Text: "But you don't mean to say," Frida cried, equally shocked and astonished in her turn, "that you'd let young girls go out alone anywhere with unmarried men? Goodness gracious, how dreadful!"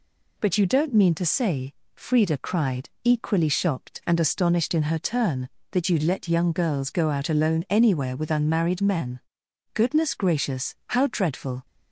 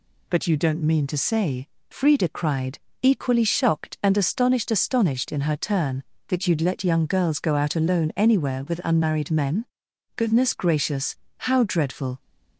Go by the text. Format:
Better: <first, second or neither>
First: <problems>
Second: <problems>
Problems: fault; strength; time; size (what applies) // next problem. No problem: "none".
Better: first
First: none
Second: says "astonished" twice; at 4.6 s